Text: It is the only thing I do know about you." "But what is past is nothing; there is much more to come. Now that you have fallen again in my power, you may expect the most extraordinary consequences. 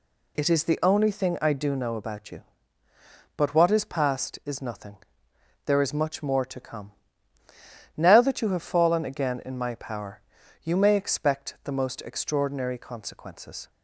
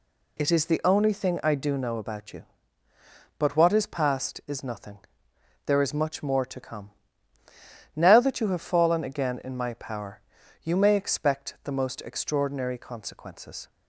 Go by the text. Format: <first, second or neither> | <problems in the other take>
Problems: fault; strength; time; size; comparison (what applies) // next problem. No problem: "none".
neither | none